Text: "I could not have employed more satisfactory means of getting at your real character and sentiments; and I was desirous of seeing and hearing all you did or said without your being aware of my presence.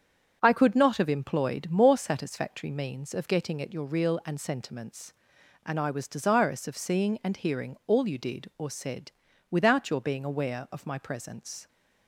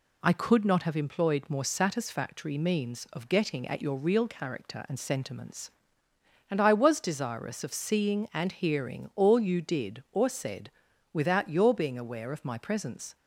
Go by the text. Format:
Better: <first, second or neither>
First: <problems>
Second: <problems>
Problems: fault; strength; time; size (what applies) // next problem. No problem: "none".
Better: second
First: starts louder than the rest; strong; until 1.4 s; 7.5 dB // skips "character"; at 4.2 s // pauses between "said" and "without"; at 9.1 s; 0.38 s long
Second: pauses between "said" and "without"; at 10.6 s; 0.42 s long